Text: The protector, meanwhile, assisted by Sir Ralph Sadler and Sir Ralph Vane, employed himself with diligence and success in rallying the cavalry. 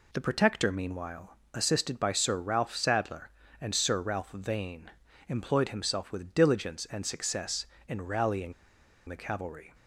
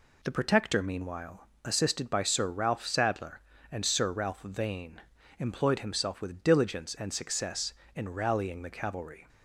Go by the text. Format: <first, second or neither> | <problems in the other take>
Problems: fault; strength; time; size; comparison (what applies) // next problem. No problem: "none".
second | pauses between "rallying" and "the"; noticeable; at 8.5 s; 0.55 s long